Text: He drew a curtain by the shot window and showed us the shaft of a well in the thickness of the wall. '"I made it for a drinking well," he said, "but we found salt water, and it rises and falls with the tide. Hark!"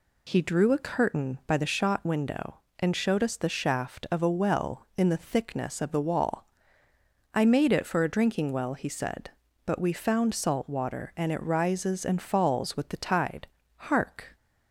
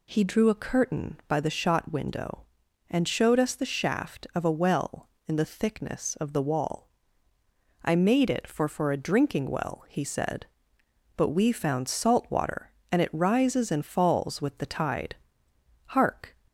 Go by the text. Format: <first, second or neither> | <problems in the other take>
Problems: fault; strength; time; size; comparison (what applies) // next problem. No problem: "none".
first | says "for" twice; at 8.6 s